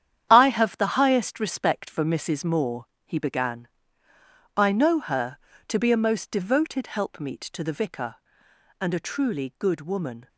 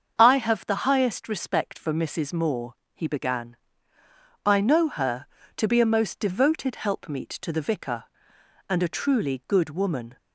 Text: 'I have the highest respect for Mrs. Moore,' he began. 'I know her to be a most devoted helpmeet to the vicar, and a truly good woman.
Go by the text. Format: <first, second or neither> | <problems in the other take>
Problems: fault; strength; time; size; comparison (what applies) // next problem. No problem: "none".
second | gets quieter; strong; throughout; 9.5 dB // starts louder than the rest; strong; until 1.3 s; 9.5 dB; also in the second